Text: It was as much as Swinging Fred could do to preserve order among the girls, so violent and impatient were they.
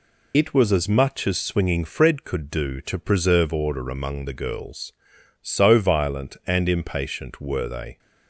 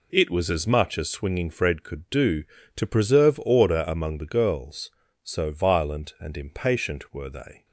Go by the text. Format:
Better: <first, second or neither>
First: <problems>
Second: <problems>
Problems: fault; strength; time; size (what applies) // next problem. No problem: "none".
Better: second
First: loses the start of "It"; at 0.3 s; 65 ms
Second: none